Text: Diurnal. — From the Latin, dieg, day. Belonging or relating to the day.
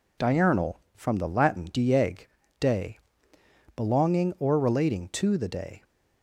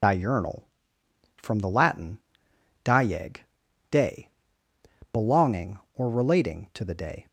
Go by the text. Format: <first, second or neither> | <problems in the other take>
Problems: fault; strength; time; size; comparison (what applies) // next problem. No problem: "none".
first | loses the start of "Diurnal"; at 0.0 s; 70 ms